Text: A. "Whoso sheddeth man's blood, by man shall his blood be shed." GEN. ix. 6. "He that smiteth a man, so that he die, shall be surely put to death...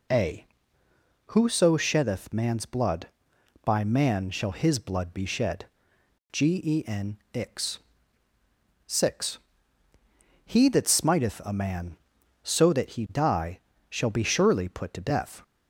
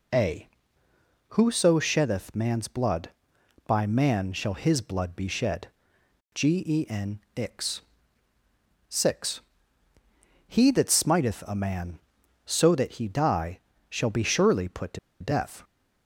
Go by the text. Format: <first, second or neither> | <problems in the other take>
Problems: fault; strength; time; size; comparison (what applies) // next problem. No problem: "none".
first | pauses between "to" and "death"; slight; at 14.9 s; 0.22 s long